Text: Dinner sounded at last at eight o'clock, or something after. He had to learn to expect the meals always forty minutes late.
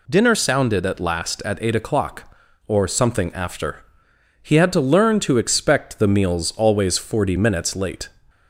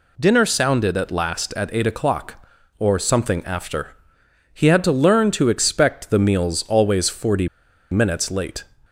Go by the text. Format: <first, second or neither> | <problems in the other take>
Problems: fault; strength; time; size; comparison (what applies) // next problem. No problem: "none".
first | pauses between "forty" and "minutes"; at 7.4 s; 0.43 s long